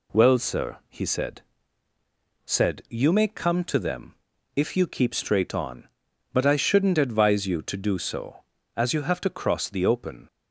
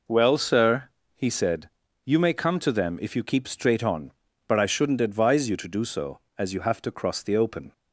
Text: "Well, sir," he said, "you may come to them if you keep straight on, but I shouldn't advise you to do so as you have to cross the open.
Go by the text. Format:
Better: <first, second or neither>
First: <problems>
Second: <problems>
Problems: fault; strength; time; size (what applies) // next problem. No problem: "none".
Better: second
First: says "said" twice; at 2.4 s // pauses between "them" and "if"; at 4.1 s; 0.42 s long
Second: none